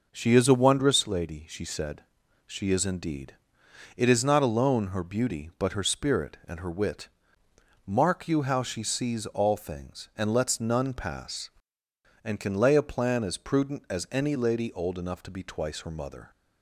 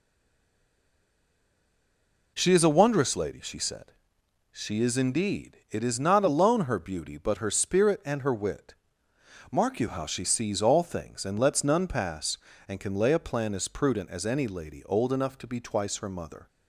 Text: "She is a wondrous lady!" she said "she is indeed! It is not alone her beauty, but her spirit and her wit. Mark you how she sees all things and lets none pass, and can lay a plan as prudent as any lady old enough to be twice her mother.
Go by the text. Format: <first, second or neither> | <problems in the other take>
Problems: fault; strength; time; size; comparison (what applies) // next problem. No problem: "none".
first | stays silent before the first word; until 2.3 s; 2.3 s long // pauses between "said" and "she"; noticeable; at 3.9 s; 0.60 s long; also in the first